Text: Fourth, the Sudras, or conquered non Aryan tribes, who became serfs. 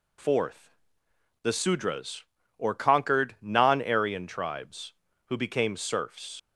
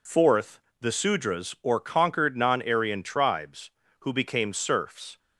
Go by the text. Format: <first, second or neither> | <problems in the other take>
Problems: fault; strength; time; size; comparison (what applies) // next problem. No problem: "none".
second | leaves "serfs" unfinished; at 6.3 s; 95 ms